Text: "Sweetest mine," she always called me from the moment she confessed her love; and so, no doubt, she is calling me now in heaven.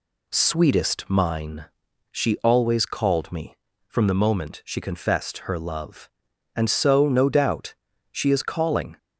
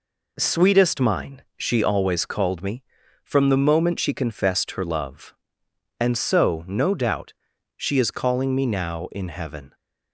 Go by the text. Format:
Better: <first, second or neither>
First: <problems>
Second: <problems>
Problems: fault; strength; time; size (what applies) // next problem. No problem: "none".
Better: second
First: stops before "me now in heaven"; at 8.9 s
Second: none